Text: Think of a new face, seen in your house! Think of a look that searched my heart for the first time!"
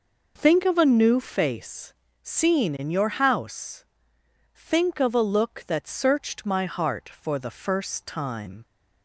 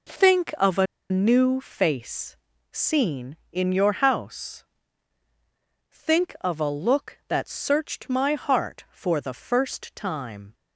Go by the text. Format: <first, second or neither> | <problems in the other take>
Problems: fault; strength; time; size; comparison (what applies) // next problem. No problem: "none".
first | pauses between "a" and "new"; slight; at 0.8 s; 0.26 s long